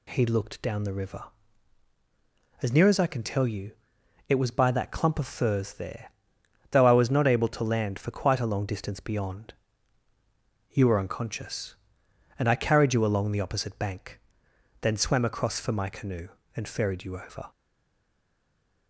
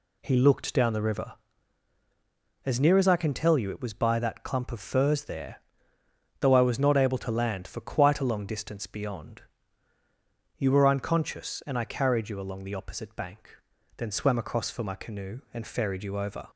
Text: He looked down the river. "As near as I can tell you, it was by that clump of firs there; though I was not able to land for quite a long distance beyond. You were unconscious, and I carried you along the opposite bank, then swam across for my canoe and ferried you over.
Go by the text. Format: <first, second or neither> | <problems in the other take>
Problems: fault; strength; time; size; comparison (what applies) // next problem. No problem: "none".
second | stays silent after the last word; noticeable; from 17.5 s on; 1.3 s long